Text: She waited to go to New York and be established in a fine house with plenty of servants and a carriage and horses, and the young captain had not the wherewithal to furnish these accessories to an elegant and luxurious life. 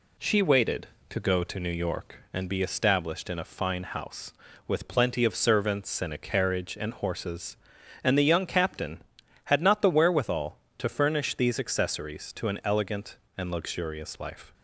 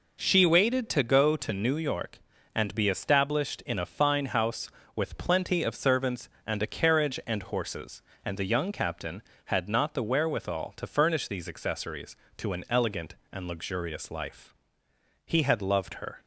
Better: first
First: none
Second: goes on to say "He had loved her"; noticeable; from 15.2 s on; 0.94 s long

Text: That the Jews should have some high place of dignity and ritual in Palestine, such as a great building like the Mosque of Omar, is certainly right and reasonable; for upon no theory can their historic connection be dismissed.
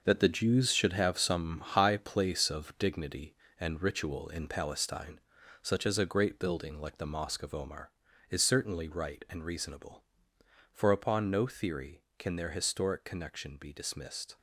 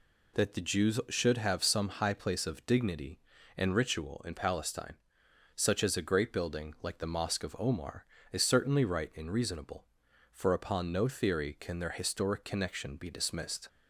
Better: second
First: gets quieter; strong; throughout; 9 dB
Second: none

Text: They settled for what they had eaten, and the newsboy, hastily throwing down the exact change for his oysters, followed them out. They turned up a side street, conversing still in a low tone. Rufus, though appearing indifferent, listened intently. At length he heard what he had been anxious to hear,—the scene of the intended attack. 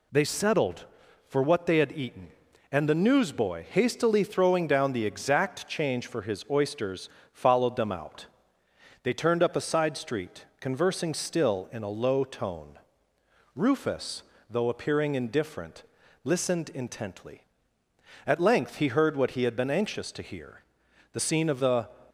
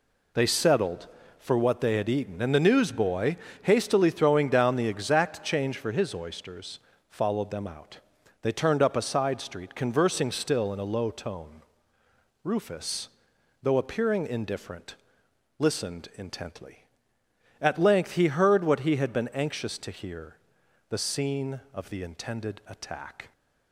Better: second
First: stops before "intended attack"; at 22.0 s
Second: none

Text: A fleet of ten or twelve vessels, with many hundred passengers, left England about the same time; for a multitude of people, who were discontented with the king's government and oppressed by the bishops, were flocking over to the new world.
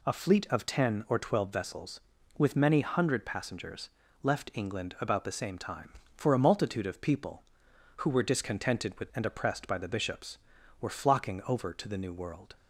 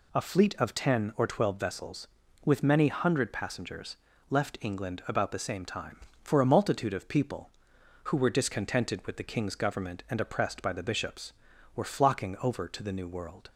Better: second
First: skips "the king's government"; at 9.1 s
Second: none

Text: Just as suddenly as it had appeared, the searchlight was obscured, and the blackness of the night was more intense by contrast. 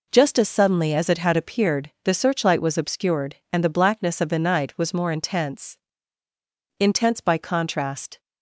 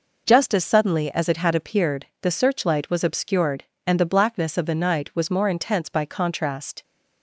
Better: second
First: says "intense" twice; at 6.7 s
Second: none

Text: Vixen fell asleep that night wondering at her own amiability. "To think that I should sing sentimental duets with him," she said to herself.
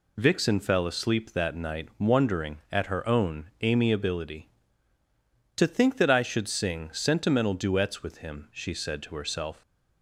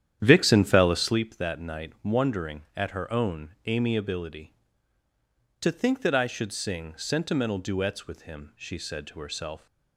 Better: first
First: none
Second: starts louder than the rest; strong; until 1.2 s; 10.5 dB

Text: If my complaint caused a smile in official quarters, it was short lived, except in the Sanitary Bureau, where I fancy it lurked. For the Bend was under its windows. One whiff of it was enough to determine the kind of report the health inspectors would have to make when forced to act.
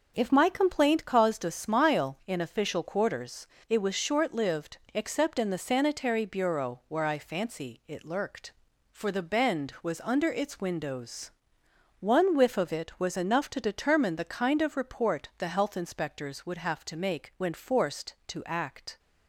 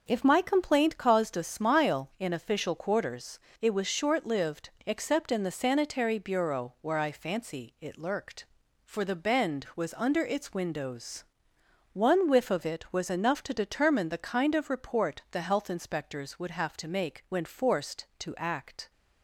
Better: neither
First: none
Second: none

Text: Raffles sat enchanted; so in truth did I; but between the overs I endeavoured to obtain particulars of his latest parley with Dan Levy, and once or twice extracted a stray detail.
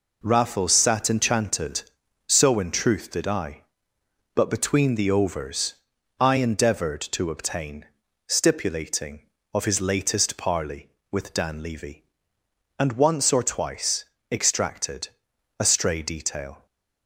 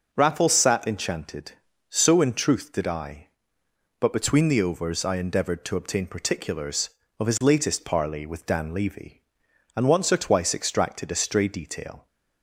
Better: second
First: pauses between "overs" and "I"; noticeable; at 5.7 s; 0.46 s long // says "stipulating" for "particulars"; at 8.2 s // pauses between "twice" and "extracted"; slight; at 14.0 s; 0.26 s long // pauses between "extracted" and "a"; noticeable; at 15.0 s; 0.50 s long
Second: none

